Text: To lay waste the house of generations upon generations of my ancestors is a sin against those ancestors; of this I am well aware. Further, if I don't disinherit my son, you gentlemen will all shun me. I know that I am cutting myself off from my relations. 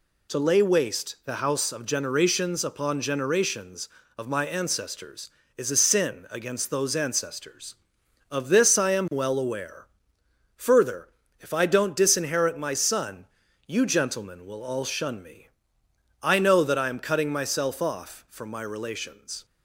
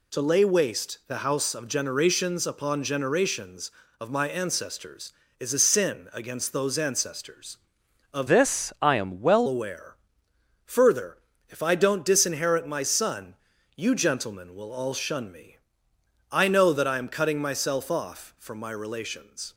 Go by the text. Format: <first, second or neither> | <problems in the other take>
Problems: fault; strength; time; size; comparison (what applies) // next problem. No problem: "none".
first | changes voice from "this" to "well"; from 8.2 to 9.4 s; 1.2 s long